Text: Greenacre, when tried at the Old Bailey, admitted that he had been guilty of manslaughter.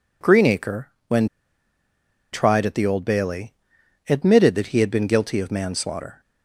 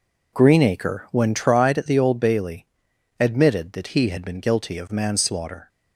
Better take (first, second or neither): second